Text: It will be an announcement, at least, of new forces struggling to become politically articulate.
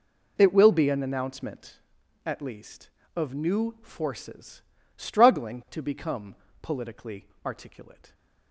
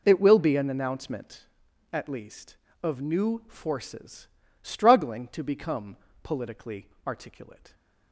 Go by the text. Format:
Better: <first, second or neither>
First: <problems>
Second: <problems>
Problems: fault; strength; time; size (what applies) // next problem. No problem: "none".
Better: neither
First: pauses between "forces" and "struggling"; slight; at 4.6 s; 0.34 s long // pauses between "become" and "politically"; slight; at 6.3 s; 0.28 s long // pauses between "politically" and "articulate"; slight; at 7.2 s; 0.18 s long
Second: pauses between "forces" and "struggling"; slight; at 4.2 s; 0.34 s long // pauses between "become" and "politically"; slight; at 5.9 s; 0.28 s long // pauses between "politically" and "articulate"; slight; at 6.8 s; 0.18 s long